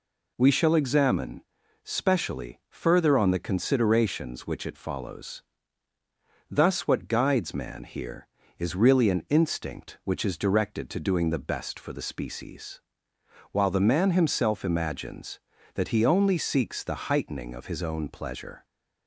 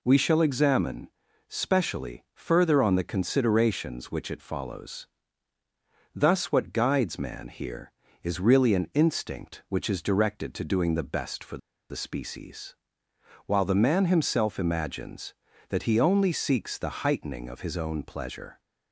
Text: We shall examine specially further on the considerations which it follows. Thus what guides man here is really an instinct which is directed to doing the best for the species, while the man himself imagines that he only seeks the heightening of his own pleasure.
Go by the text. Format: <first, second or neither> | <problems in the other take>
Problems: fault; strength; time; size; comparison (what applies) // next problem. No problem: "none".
first | pauses between "examine" and "specially"; at 1.0 s; 0.38 s long; also in the first // pauses between "for" and "the"; slight; at 11.5 s; 0.33 s long